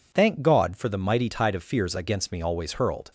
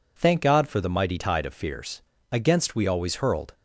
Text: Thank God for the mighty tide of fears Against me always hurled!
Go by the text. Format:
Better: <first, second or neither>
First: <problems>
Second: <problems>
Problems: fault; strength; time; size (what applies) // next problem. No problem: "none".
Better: first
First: none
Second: pauses between "fears" and "Against"; slight; at 1.9 s; 0.30 s long // says "we" for "me"; at 2.7 s